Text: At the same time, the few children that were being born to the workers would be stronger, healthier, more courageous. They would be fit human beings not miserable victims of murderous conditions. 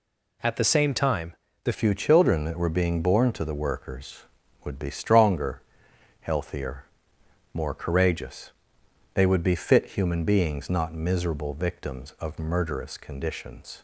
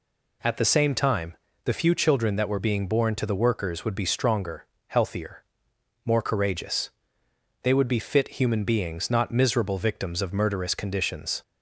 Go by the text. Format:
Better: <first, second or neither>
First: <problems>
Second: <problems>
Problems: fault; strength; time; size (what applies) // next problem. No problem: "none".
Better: second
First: changes voice at "few"; from 1.7 s on; 12.1 s long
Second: none